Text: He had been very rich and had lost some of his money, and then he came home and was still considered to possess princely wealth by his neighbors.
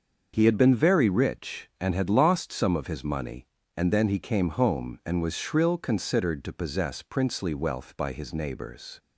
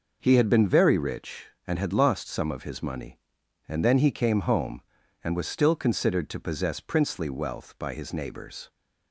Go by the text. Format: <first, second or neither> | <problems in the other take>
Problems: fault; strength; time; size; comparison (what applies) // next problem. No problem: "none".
second | starts louder than the rest; until 1.3 s; 6.5 dB // says "shrill" for "still"; at 5.3 s